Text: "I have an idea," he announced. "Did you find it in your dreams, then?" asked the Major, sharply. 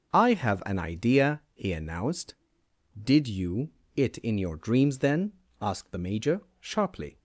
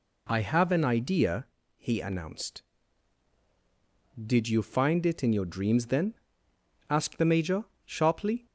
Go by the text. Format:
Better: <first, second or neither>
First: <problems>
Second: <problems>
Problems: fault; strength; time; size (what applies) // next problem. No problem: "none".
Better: second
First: skips "find"; at 3.8 s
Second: none